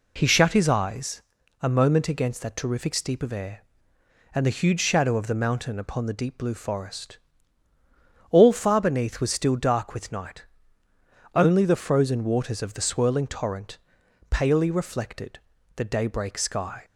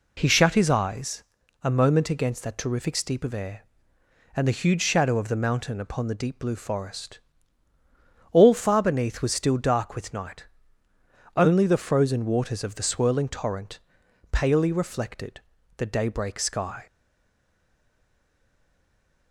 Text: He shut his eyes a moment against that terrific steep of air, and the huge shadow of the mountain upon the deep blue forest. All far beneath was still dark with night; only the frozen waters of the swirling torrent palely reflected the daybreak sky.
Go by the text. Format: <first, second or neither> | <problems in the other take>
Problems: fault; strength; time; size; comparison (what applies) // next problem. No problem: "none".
first | pauses between "eyes" and "a"; at 1.2 s; 0.40 s long; also in the first // pauses between "torrent" and "palely"; noticeable; at 13.7 s; 0.54 s long; noticeable in the first // pauses between "reflected" and "the"; slight; at 15.3 s; 0.36 s long; slight in the first // stays silent after the last word; from 16.8 s on; 2.5 s long